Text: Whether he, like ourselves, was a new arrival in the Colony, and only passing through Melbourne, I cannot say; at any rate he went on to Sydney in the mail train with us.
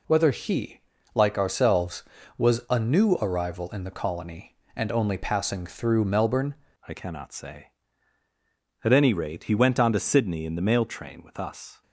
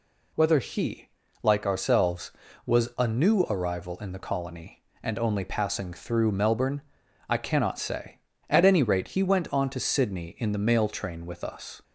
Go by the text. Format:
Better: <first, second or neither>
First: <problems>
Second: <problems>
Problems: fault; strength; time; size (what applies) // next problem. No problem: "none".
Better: second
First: changes voice at "I"; from 6.8 s on; 5.0 s long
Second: none